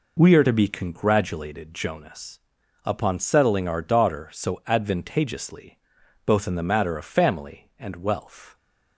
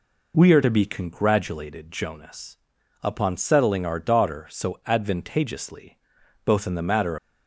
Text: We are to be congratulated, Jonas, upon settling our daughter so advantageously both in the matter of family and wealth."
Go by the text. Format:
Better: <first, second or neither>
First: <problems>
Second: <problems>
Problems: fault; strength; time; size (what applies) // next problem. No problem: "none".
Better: first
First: pauses between "advantageously" and "both"; noticeable; at 5.7 s; 0.48 s long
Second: pauses between "advantageously" and "both"; noticeable; at 5.9 s; 0.48 s long // stops before "of family and wealth"; at 7.1 s